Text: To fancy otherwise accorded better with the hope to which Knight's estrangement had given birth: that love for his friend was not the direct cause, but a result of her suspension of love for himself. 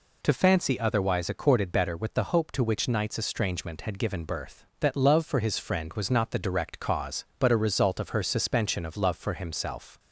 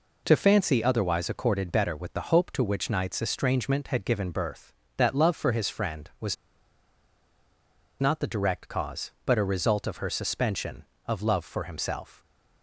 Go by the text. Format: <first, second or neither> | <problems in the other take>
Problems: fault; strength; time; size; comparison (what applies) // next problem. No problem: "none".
first | pauses between "was" and "not"; strong; at 6.3 s; 1.6 s long